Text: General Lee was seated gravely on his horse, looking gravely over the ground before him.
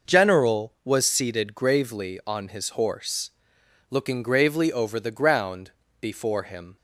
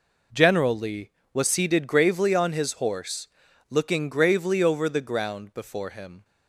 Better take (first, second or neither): second